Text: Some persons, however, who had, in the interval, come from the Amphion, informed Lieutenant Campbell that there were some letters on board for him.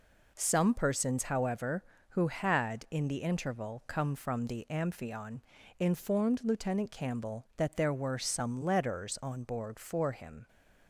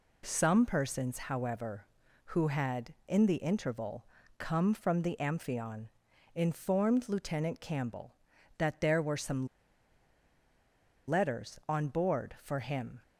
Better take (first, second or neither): first